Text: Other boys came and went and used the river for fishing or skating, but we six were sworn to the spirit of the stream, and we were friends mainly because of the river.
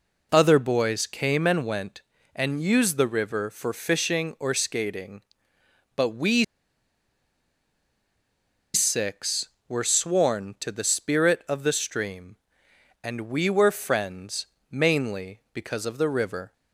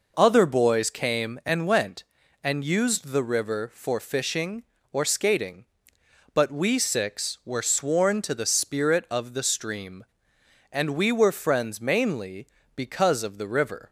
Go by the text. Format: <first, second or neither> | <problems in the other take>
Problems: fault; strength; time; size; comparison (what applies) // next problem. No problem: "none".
second | pauses between "we" and "six"; strong; at 6.4 s; 2.3 s long // pauses between "friends" and "mainly"; slight; at 14.4 s; 0.24 s long